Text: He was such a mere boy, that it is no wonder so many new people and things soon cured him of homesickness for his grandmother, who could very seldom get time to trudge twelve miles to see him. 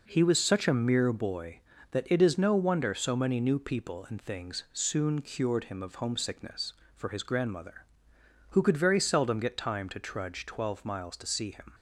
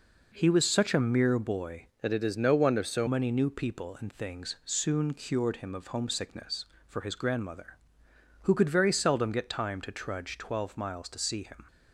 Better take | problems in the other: first | changes voice from "that" to "so"; from 2.0 to 3.0 s; 1.0 s long

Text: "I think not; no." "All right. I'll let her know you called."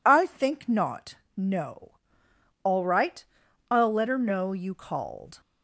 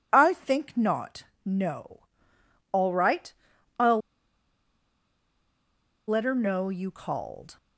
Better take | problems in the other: first | pauses between "I'll" and "let"; strong; at 3.9 s; 2.0 s long

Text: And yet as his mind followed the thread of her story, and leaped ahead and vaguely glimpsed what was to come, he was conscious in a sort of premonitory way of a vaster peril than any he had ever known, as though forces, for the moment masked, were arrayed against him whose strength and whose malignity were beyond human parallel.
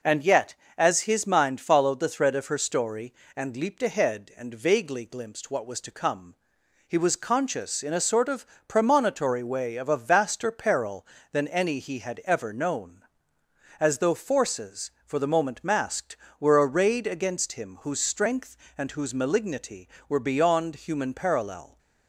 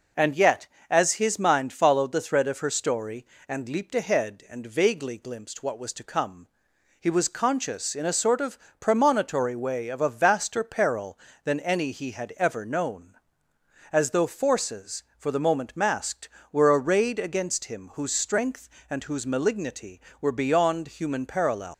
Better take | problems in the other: first | pauses between "of" and "premonitory"; slight; at 8.5 s; 0.22 s long; slight in the first // leaves "parallel" unfinished; at 21.7 s; 160 ms

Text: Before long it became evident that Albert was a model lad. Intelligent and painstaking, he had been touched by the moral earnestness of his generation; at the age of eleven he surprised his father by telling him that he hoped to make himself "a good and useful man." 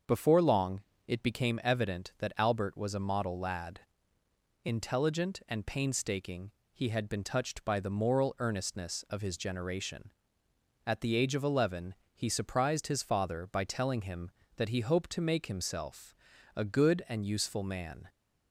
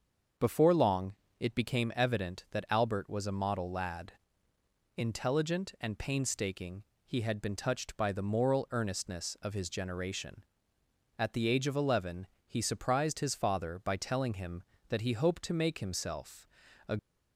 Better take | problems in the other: first | starts louder than the rest; until 1.6 s; 6.5 dB; also in the first // pauses between "long" and "it"; slight; at 1.1 s; 0.26 s long; slight in the first // pauses between "eleven" and "he"; slight; at 12.2 s; 0.18 s long; slight in the first // pauses between "himself" and "a"; at 16.4 s; 0.40 s long; also in the first // stops before "good and useful man"; at 16.9 s

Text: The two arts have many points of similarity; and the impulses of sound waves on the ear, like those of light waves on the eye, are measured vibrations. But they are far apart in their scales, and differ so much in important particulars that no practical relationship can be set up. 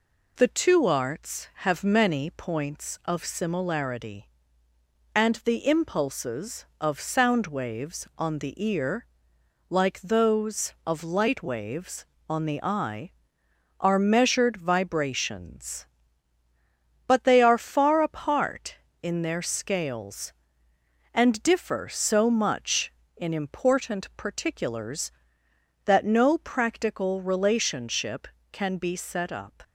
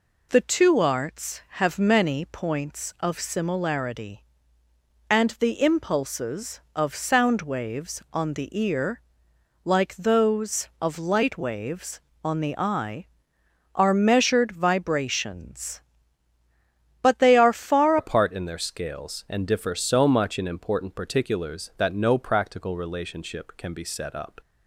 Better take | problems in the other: first | changes voice at "apart"; from 17.9 s on; 6.4 s long

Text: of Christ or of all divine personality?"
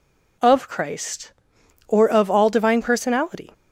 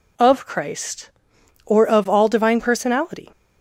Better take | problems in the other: neither | none

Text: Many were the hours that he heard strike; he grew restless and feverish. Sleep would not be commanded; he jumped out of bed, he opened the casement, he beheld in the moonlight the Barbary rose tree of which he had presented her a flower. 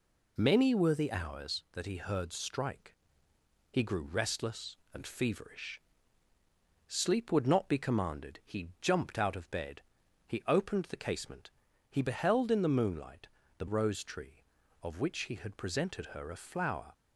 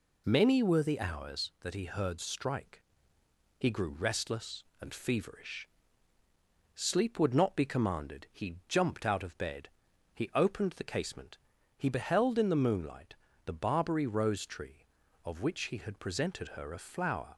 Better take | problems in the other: second | pauses between "moonlight" and "the"; slight; at 13.2 s; 0.30 s long; slight in the second // skips "Barbary"; at 13.6 s

